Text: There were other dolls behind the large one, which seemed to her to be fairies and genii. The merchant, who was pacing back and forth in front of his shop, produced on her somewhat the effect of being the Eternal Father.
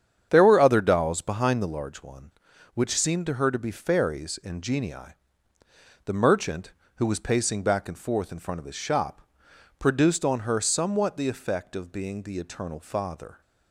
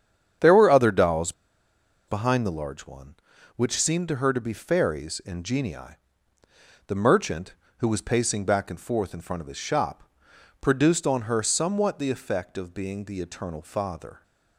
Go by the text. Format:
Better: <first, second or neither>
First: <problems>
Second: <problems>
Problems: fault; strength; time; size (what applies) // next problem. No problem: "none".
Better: first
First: starts louder than the rest; strong; until 1.3 s; 8 dB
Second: starts louder than the rest; strong; until 2.1 s; 8 dB // pauses between "dolls" and "behind"; noticeable; at 1.3 s; 0.76 s long